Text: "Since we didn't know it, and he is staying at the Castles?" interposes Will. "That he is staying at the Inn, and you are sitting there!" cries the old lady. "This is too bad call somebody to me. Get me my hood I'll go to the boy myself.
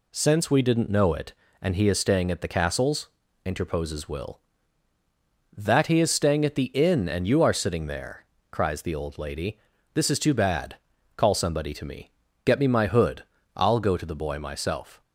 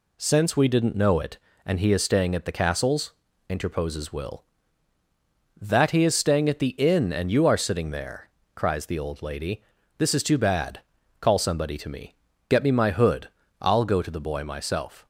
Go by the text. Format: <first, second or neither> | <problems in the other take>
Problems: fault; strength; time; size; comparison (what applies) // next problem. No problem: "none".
neither | pauses between "bad" and "call"; the same in both // pauses between "hood" and "I'll"; slight; the same in both